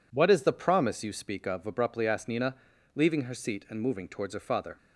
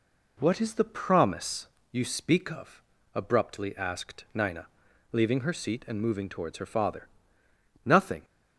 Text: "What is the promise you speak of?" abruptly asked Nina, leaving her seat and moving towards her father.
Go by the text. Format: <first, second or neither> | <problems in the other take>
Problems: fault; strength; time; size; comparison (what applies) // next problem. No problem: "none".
first | pauses between "promise" and "you"; slight; at 1.6 s; 0.24 s long // goes on to say "Nothing"; slight; from 7.8 s on; 0.38 s long